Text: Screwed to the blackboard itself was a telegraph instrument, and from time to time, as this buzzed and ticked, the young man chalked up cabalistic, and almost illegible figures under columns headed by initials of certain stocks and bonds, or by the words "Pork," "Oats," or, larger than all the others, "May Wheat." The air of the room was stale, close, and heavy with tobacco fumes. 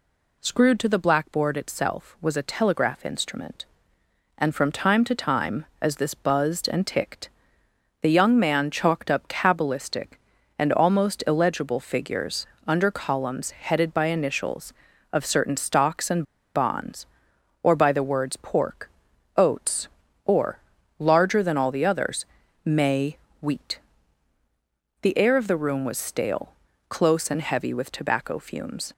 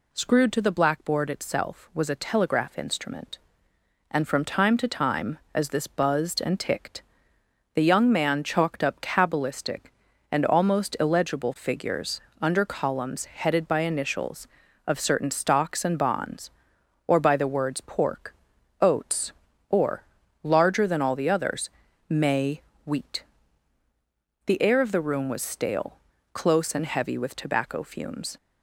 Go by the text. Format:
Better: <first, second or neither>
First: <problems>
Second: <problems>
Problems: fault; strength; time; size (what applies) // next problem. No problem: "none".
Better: second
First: pauses between "figures" and "under"; slight; at 12.4 s; 0.20 s long // pauses between "and" and "bonds"; slight; at 16.2 s; 0.31 s long // pauses between "May" and "Wheat"; slight; at 23.1 s; 0.22 s long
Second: pauses between "figures" and "under"; slight; at 12.2 s; 0.20 s long // pauses between "May" and "Wheat"; slight; at 22.6 s; 0.22 s long